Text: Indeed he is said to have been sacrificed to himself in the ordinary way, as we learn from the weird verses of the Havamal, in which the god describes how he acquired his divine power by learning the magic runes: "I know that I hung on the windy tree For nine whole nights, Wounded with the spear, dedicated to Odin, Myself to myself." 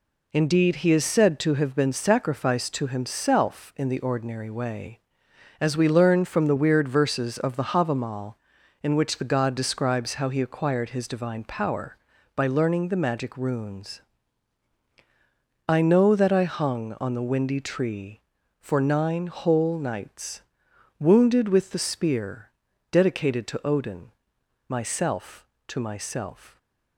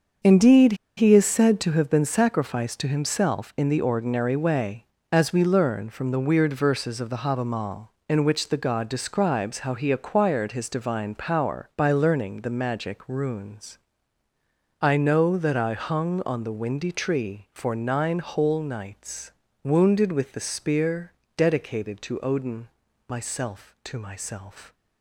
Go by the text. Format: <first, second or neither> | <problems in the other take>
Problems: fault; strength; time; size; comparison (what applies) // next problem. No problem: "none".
first | starts louder than the rest; until 1.4 s; 6.5 dB // pauses between "Indeed" and "he"; slight; at 0.7 s; 0.23 s long